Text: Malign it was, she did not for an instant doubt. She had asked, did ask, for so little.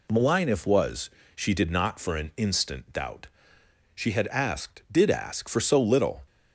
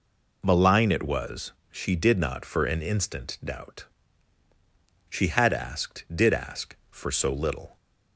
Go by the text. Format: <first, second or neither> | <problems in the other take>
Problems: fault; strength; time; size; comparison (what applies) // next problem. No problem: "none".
second | says "if" for "it"; at 0.4 s